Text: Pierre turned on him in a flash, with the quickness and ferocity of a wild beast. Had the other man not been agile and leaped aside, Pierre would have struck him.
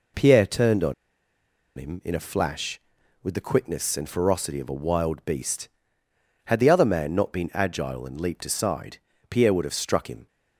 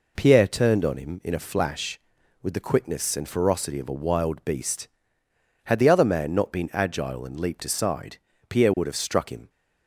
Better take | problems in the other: second | pauses between "on" and "him"; noticeable; at 0.9 s; 0.82 s long

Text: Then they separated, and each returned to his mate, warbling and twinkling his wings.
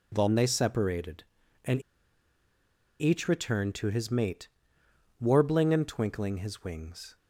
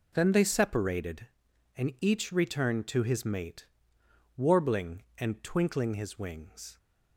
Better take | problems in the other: second | pauses between "and" and "each"; at 1.8 s; 1.1 s long

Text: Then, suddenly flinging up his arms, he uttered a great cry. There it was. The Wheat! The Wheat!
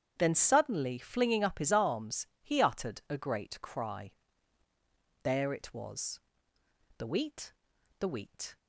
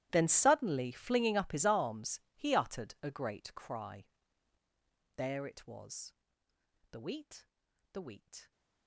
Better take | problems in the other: first | gets quieter; strong; throughout; 24 dB // starts louder than the rest; strong; until 1.1 s; 14 dB; strong in the first

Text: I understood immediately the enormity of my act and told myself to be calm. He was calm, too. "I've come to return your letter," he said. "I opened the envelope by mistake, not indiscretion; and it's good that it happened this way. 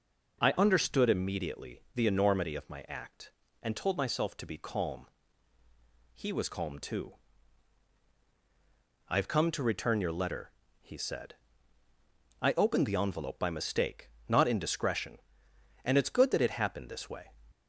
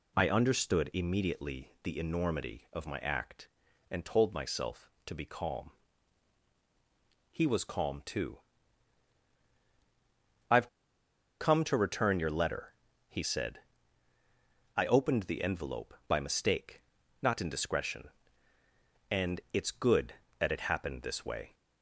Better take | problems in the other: first | pauses between "I've" and "come"; noticeable; at 10.6 s; 0.73 s long

